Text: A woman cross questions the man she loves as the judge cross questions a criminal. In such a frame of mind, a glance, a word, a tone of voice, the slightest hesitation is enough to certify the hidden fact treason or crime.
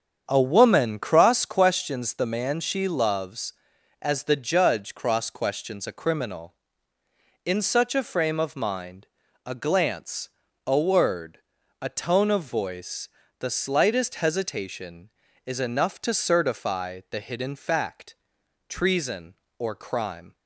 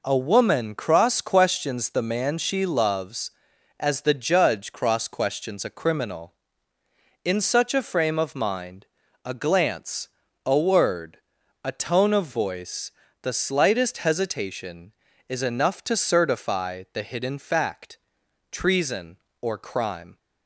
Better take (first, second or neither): second